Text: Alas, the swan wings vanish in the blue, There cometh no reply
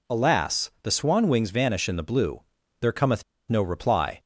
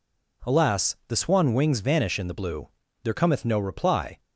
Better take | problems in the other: second | pauses between "cometh" and "no"; slight; at 3.2 s; 0.26 s long

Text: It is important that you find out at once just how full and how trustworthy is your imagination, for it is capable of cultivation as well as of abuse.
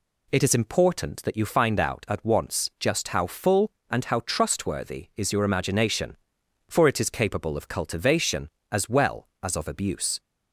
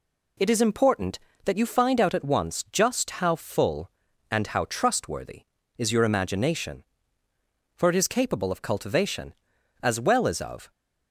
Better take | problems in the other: first | stops before "abuse"; at 10.7 s

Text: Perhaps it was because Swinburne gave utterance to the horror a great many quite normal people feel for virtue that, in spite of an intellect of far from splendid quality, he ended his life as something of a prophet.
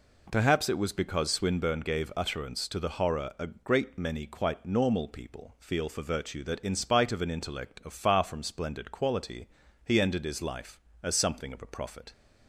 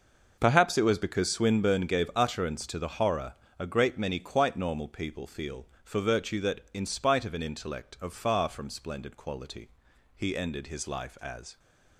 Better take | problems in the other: first | pauses between "horror" and "a"; slight; at 3.3 s; 0.24 s long // stops before "something of a prophet"; at 11.5 s

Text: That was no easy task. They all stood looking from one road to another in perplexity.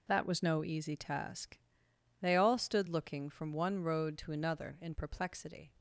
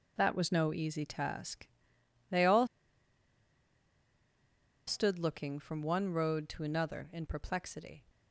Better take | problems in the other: first | pauses between "all" and "stood"; strong; at 2.6 s; 2.2 s long

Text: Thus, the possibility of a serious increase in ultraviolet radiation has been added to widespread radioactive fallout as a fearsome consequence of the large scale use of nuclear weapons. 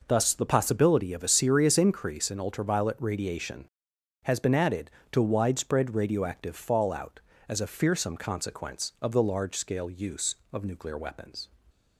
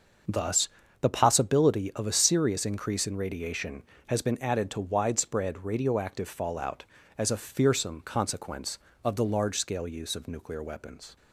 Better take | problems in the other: first | starts louder than the rest; until 1.6 s; 6.5 dB // skips "ultraviolet"; at 3.1 s

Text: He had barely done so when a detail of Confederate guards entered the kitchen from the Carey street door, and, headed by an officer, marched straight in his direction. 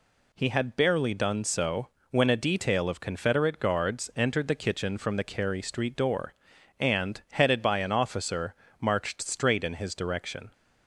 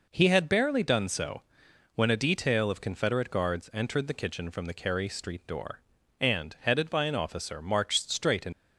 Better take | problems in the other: first | pauses between "so" and "when"; noticeable; at 1.4 s; 0.54 s long; slight in the first // stops before "his direction"; at 8.5 s

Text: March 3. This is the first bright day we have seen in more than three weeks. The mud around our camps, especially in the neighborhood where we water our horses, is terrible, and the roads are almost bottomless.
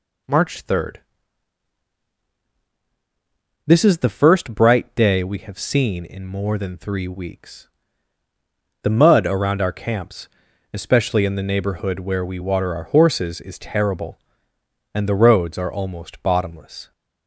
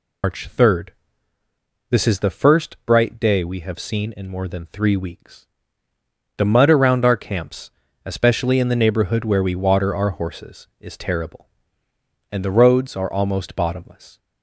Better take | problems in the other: first | loses the start of "March"; at 0.2 s; 130 ms

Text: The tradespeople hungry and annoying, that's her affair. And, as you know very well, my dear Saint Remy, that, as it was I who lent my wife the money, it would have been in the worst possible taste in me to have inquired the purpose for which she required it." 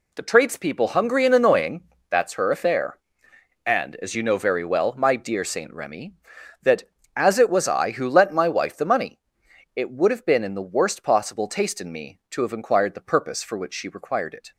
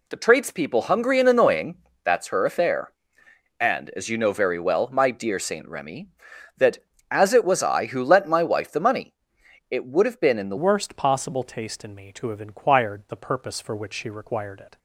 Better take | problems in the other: first | changes voice at "worst"; from 10.5 s on; 4.2 s long

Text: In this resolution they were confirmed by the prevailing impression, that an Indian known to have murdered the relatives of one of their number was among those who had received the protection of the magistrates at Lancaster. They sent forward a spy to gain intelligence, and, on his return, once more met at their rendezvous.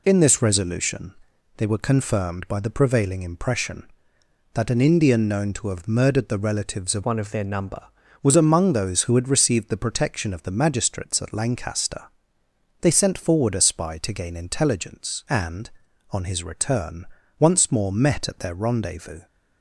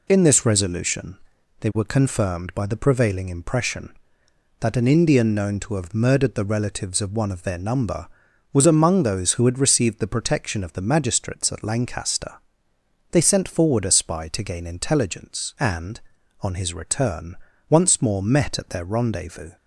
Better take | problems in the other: second | pauses between "resolution" and "they"; at 1.1 s; 0.44 s long; also in the second // changes voice from "one" to "number"; from 7.0 to 7.8 s; 0.8 s long

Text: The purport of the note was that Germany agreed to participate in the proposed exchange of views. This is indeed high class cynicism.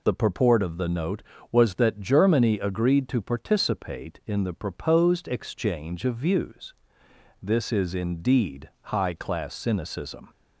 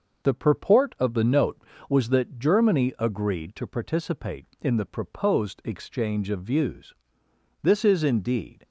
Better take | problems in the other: first | stops before "high class cynicism"; at 8.6 s

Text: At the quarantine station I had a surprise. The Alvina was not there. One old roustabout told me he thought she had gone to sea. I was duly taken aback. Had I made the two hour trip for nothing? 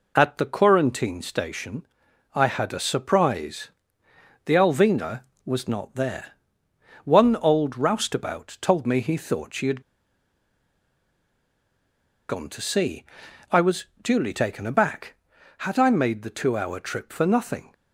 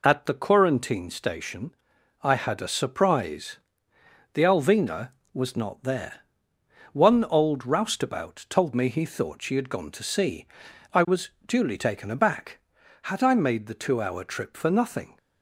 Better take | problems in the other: second | pauses between "station" and "I"; noticeable; at 1.8 s; 0.48 s long; noticeable in the second // pauses between "had" and "gone"; strong; at 9.8 s; 2.4 s long // pauses between "was" and "duly"; slight; at 13.8 s; 0.16 s long; slight in the second

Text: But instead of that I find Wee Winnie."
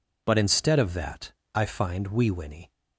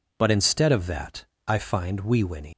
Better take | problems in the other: first | pauses between "that" and "I"; slight; at 1.2 s; 0.20 s long; slight in the first // leaves "Winnie" unfinished; at 2.5 s; 115 ms

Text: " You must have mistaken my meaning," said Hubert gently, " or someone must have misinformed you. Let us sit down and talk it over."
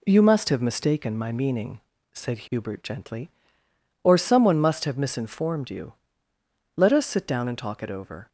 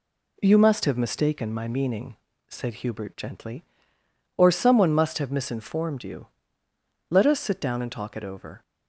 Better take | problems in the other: neither | none

